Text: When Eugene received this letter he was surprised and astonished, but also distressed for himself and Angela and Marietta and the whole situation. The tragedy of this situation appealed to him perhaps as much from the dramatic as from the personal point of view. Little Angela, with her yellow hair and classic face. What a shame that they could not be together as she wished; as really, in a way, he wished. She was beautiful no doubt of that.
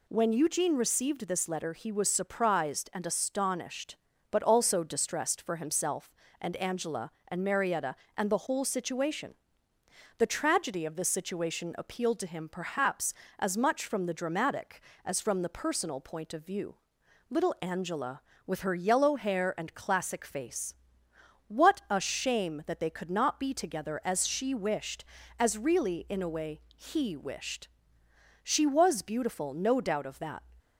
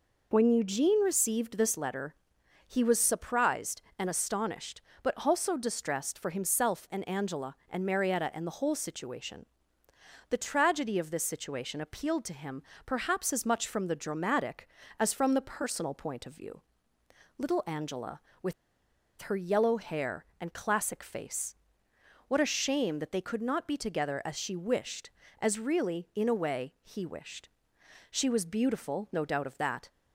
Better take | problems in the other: first | pauses between "letter" and "he"; noticeable; at 2.1 s; 0.52 s long // pauses between "him" and "perhaps"; slight; at 12.6 s; 0.24 s long // pauses between "with" and "her"; noticeable; at 18.5 s; 0.68 s long

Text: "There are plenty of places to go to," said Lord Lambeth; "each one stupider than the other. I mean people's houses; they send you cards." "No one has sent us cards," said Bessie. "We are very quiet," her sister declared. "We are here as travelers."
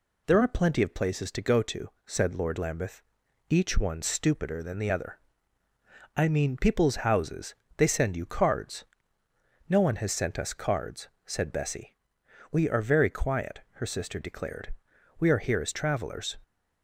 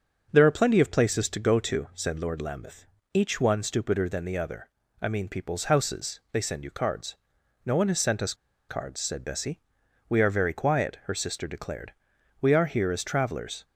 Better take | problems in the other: first | starts louder than the rest; until 1.3 s; 6.5 dB // pauses between "us" and "cards"; slight; at 8.3 s; 0.35 s long

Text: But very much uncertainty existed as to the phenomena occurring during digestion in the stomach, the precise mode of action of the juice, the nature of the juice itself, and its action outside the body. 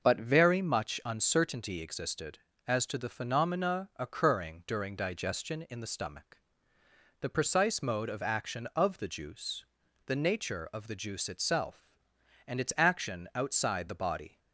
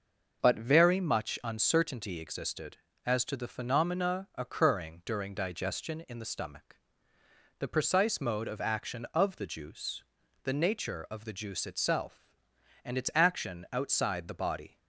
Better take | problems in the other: neither | starts louder than the rest; noticeable; the same in both

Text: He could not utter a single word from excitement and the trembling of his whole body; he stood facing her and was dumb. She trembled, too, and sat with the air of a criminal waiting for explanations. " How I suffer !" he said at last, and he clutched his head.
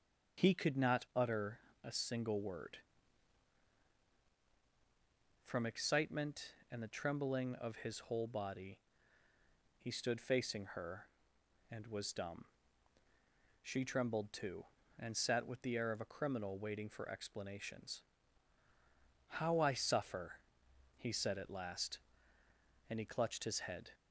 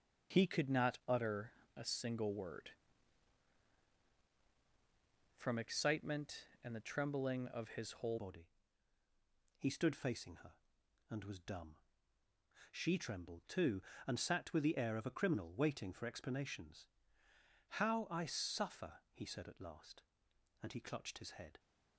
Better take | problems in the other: first | starts louder than the rest; until 1.4 s; 6 dB; also in the first // pauses between "utter" and "a"; slight; at 1.5 s; 0.24 s long; slight in the first // changes voice at "body"; from 8.1 s on; 13.4 s long

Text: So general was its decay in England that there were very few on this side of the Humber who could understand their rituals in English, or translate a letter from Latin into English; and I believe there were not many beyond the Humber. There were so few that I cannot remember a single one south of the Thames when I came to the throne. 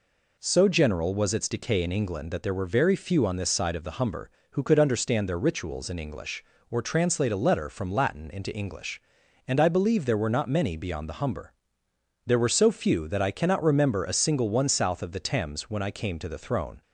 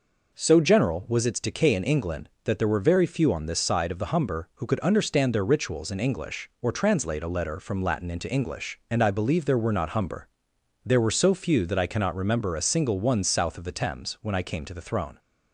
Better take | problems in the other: first | skips "many beyond the"; at 9.9 s

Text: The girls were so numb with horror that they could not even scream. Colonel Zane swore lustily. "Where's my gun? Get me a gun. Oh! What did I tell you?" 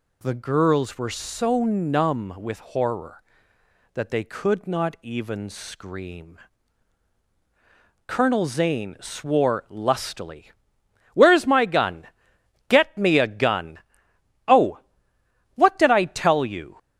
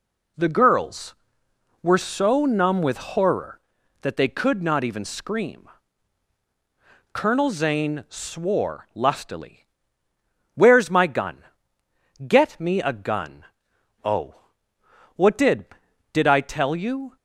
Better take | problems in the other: first | says "did" twice; at 16.1 s

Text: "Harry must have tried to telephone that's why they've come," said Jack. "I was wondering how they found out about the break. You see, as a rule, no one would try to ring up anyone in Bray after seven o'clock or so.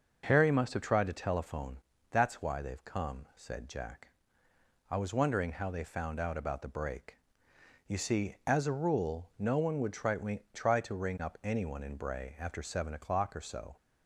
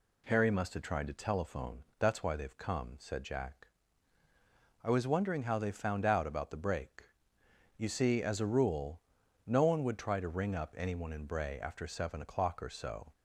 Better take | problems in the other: second | starts louder than the rest; until 1.2 s; 6 dB // pauses between "telephone" and "that's"; slight; at 1.7 s; 0.34 s long; slight in the second // says "try" twice; at 10.5 s

